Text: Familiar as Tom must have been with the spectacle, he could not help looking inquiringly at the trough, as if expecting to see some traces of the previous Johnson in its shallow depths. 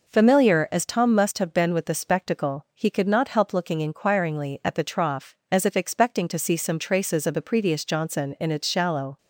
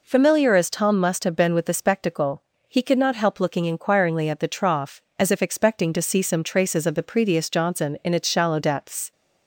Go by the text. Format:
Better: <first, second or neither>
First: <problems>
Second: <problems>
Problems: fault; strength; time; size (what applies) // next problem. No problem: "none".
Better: second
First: stops before "depths"; at 9.1 s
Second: none